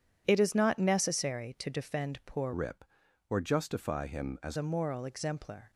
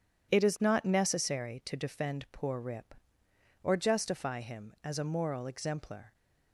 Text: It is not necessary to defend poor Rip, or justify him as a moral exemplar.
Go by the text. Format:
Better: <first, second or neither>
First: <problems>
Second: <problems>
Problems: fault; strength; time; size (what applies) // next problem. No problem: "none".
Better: second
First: changes voice from "Rip" to "as"; from 2.5 to 4.5 s; 2.0 s long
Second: none